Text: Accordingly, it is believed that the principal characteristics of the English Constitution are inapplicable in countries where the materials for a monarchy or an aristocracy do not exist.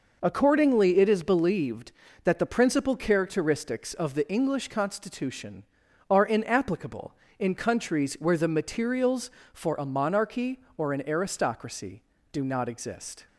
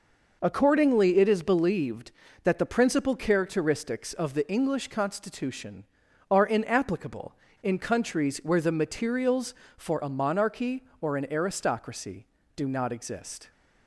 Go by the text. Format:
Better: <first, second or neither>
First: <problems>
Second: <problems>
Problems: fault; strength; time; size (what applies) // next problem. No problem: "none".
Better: neither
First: none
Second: none